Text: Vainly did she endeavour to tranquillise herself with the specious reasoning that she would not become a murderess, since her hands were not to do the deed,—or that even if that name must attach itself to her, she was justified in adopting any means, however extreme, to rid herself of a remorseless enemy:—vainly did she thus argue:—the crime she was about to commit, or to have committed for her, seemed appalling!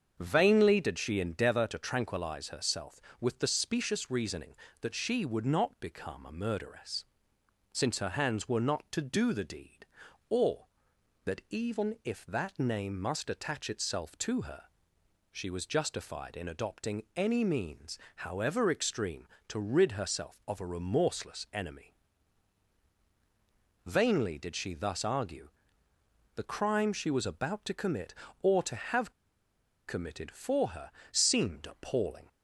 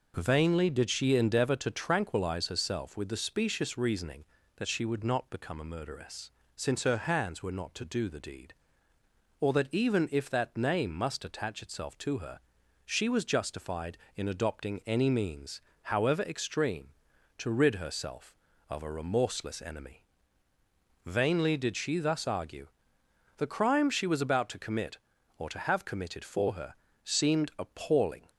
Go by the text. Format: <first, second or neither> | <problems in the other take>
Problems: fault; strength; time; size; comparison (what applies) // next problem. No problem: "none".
second | starts louder than the rest; until 1.2 s; 7 dB // pauses between "have" and "committed"; noticeable; at 29.1 s; 0.75 s long